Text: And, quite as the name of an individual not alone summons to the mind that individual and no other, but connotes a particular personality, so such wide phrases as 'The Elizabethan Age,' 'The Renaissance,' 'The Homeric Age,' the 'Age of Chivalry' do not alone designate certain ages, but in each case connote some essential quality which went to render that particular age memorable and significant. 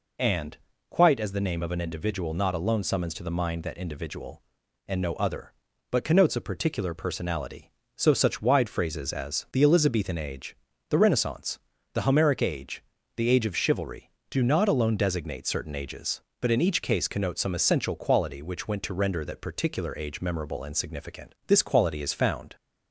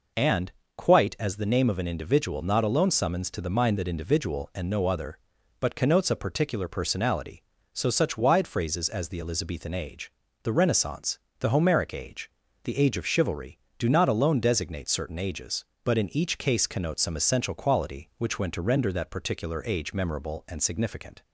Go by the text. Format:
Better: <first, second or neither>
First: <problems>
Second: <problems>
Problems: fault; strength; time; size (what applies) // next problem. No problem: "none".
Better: second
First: goes on to say "This quality is found"; noticeable; from 21.4 s on; 1.0 s long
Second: none